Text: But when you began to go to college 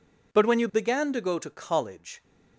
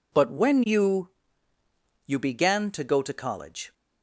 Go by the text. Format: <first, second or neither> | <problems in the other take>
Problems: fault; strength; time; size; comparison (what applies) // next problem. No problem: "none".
first | says "you" twice; at 2.0 s